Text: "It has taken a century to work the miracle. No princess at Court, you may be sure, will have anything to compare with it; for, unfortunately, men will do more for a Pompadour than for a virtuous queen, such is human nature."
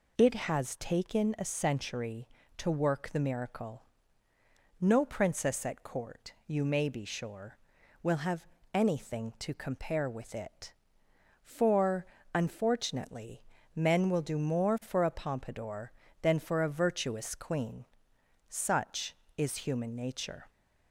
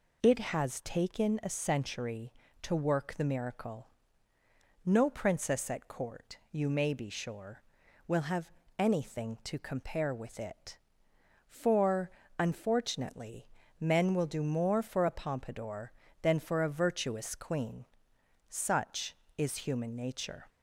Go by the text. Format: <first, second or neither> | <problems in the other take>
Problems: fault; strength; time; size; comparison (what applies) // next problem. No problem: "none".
neither | pauses between "have" and "anything"; slight; the same in both